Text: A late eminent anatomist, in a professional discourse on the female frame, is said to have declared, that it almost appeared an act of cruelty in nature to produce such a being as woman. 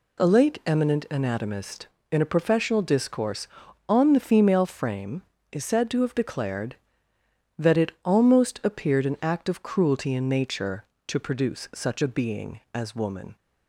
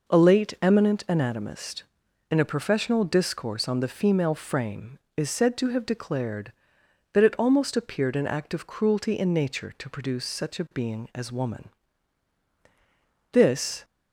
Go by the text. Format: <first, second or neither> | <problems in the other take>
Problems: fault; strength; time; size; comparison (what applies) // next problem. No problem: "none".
first | goes on to say "This"; from 13.3 s on; 0.52 s long